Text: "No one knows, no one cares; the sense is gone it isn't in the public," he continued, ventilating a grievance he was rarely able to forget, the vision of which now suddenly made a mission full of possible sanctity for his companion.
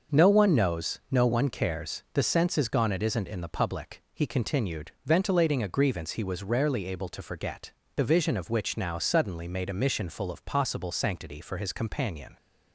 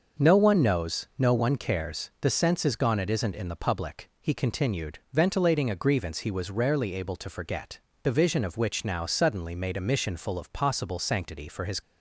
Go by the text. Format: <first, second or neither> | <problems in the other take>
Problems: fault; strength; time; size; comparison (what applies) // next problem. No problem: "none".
first | starts louder than the rest; until 1.3 s; 6.5 dB; also in the first // stops before "companion"; at 11.8 s